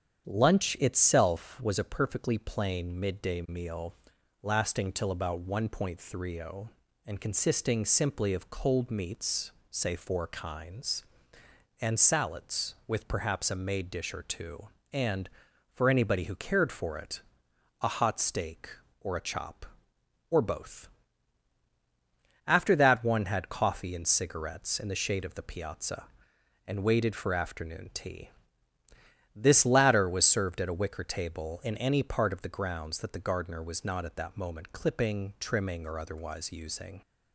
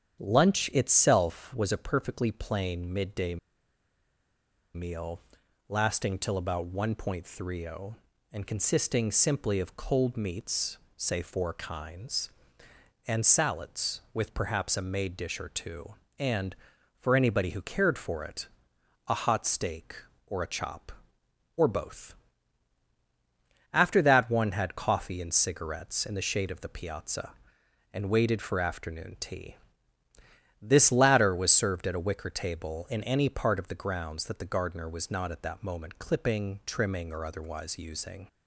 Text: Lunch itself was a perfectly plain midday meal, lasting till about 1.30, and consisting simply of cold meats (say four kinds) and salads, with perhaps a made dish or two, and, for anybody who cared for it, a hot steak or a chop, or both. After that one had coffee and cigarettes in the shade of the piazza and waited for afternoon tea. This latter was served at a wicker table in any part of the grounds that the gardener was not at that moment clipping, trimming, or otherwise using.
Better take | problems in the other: first | starts louder than the rest; strong; until 1.2 s; 8.5 dB; strong in the first // pauses between "midday" and "meal"; strong; at 3.3 s; 1.3 s long

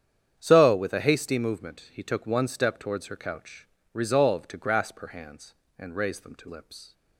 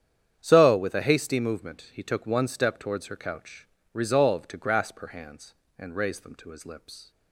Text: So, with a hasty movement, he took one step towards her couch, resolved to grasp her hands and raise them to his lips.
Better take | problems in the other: second | starts louder than the rest; strong; until 1.3 s; 8.5 dB; strong in the second // skips "his"; at 6.4 s

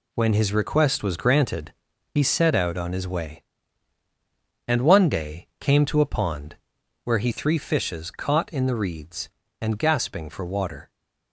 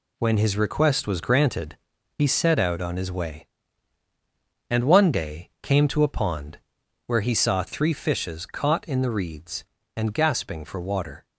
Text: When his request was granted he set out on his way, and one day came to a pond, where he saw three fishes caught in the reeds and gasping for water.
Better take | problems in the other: second | pauses between "granted" and "he"; at 1.7 s; 0.40 s long; also in the second // skips "saw"; at 7.3 s

